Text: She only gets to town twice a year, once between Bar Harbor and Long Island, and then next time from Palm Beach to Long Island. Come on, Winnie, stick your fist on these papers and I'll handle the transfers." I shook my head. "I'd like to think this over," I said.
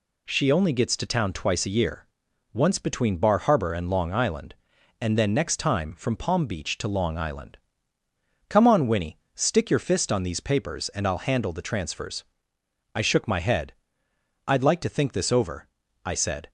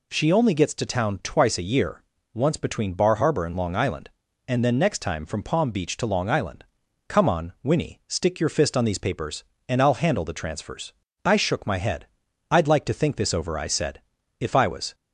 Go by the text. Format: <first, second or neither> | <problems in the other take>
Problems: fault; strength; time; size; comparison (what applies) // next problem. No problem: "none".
first | goes on to say "If I was"; from 14.4 s on; 0.54 s long